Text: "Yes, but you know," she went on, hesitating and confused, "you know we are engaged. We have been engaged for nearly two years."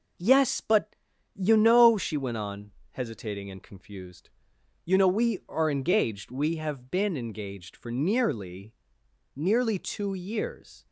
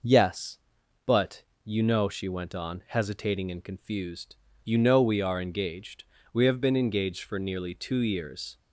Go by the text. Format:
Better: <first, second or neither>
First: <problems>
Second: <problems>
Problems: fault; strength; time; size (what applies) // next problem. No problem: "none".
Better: second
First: pauses between "but" and "you"; at 0.9 s; 0.38 s long // says "nearly" twice; at 9.3 s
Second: pauses between "but" and "you"; slight; at 1.4 s; 0.20 s long